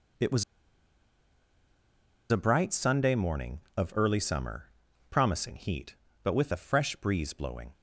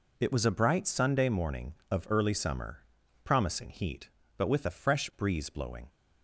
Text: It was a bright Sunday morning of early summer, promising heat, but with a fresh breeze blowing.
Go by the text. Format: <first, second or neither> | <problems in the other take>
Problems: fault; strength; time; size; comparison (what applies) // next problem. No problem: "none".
second | pauses between "was" and "a"; strong; at 0.4 s; 1.8 s long